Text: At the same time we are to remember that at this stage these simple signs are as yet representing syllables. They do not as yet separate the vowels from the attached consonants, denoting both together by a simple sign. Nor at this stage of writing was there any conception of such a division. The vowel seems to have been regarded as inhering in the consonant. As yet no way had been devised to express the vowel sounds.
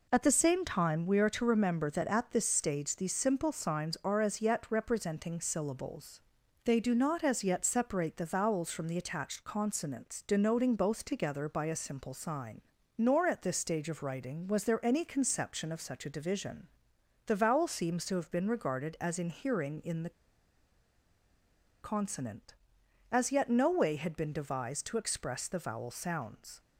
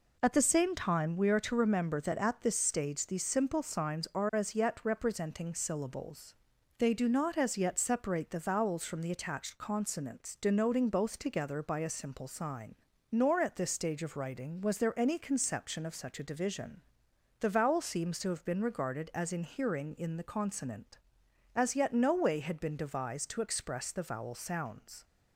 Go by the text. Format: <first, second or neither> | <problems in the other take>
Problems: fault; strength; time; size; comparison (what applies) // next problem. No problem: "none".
second | pauses between "the" and "consonant"; strong; at 20.0 s; 1.7 s long